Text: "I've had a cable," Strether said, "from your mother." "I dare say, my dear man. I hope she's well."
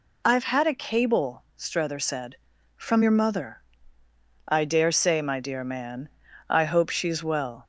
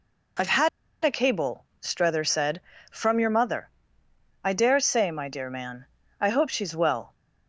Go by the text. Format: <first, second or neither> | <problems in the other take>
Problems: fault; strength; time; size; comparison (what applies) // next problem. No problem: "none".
first | pauses between "had" and "a"; slight; at 0.6 s; 0.33 s long